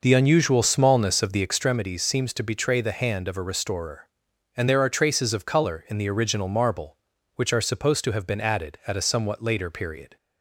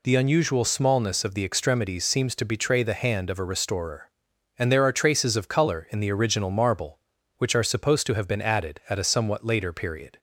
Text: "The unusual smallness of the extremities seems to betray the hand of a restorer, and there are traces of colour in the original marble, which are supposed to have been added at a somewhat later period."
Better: second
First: starts louder than the rest; noticeable; until 1.6 s; 5.5 dB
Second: none

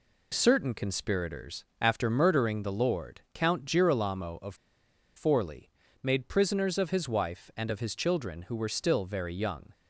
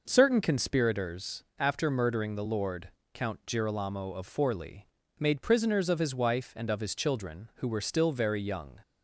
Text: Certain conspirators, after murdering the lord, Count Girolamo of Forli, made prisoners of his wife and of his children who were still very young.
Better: second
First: pauses between "of" and "Forli"; noticeable; at 4.5 s; 0.61 s long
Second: none

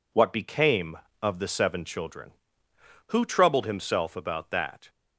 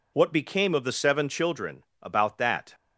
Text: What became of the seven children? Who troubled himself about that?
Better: first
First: none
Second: skips "Who troubled himself"; at 1.9 s

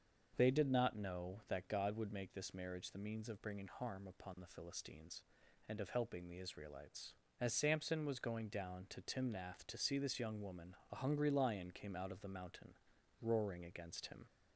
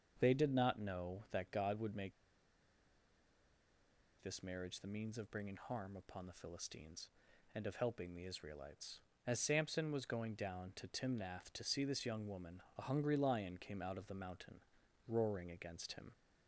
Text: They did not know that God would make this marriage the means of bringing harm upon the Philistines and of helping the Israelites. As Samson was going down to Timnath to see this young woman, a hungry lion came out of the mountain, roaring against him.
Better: first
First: starts louder than the rest; until 1.3 s; 6.5 dB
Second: starts louder than the rest; until 1.2 s; 6.5 dB // pauses between "make" and "this"; strong; at 2.1 s; 2.0 s long

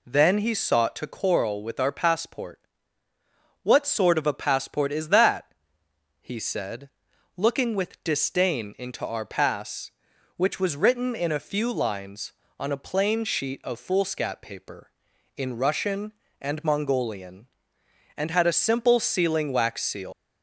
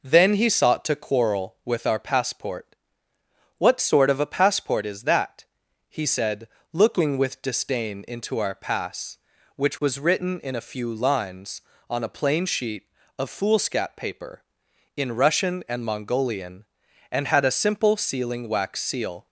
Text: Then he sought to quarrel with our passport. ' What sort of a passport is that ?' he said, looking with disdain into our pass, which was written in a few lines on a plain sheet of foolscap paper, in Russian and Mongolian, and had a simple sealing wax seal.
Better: second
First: leaves "seal" unfinished; at 20.1 s; 160 ms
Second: none

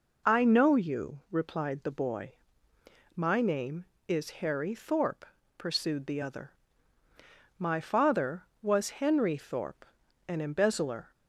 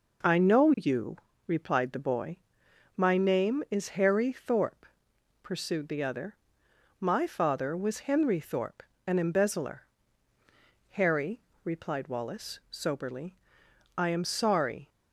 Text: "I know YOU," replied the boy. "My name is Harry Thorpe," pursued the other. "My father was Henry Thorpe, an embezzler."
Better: first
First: none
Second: goes on to say "Harry replied Wallace soberly I am sorry"; strong; from 10.9 s on; 3.9 s long

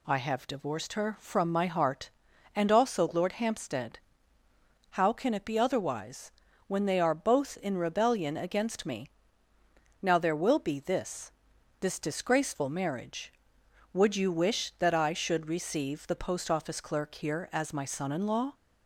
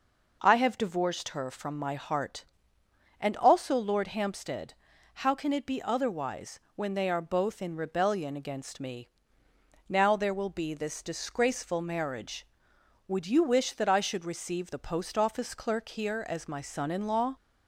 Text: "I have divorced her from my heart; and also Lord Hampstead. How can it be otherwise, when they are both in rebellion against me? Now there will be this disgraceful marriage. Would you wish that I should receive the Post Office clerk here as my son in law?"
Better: second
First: says "this" twice; at 11.7 s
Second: none

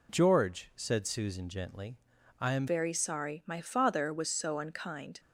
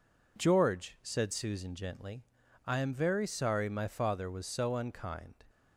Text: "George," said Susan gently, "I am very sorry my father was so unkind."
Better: second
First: changes voice at "very"; from 2.6 s on; 2.5 s long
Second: none

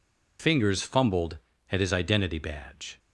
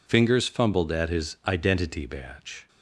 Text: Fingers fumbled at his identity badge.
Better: neither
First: none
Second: none

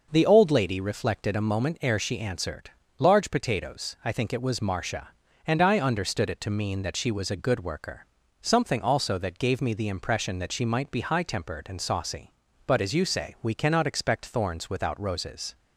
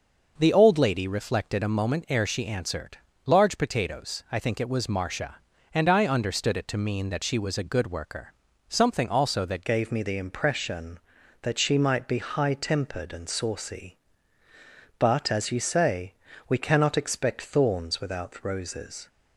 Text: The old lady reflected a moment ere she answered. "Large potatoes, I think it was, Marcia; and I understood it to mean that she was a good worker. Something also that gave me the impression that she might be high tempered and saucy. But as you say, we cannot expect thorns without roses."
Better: first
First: none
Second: changes voice at "gave"; from 9.6 s on; 9.4 s long

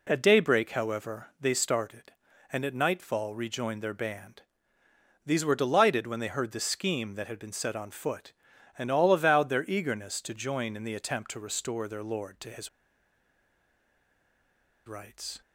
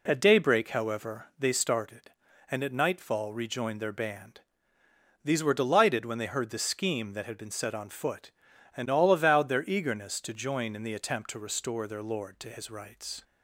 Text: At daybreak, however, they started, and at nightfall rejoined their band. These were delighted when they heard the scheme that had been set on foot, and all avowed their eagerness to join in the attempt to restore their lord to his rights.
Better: second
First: pauses between "his" and "rights"; strong; at 12.6 s; 2.1 s long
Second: none

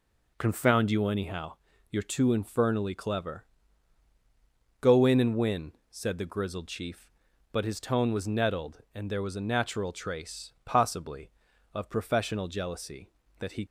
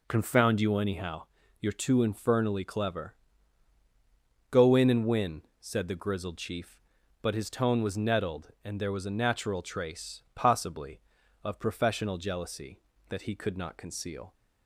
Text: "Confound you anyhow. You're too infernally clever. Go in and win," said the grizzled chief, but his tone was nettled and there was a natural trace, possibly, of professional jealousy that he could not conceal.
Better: second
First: stops before "could not conceal"; at 13.6 s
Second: none

